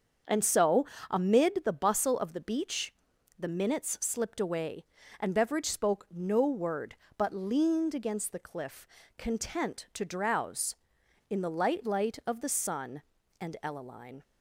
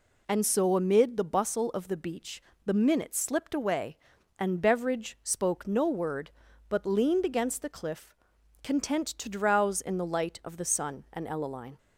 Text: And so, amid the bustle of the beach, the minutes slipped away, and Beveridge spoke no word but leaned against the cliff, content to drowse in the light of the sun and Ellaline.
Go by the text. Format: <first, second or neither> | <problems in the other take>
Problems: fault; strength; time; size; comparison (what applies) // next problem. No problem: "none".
second | starts louder than the rest; until 1.5 s; 7 dB // says "light" twice; at 11.8 s